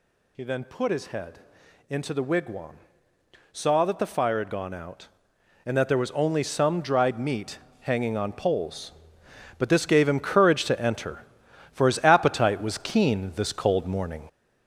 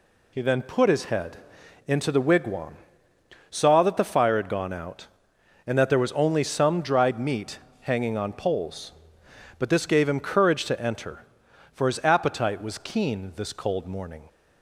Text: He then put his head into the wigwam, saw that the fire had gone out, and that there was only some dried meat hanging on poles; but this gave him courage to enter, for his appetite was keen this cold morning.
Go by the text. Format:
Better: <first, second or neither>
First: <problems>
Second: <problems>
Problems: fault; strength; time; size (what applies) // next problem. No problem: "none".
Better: second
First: gets louder; noticeable; throughout; 6 dB // pauses between "head" and "into"; noticeable; at 1.3 s; 0.50 s long // pauses between "meat" and "hanging"; slight; at 7.5 s; 0.22 s long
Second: pauses between "head" and "into"; noticeable; at 1.3 s; 0.50 s long // pauses between "meat" and "hanging"; slight; at 7.5 s; 0.22 s long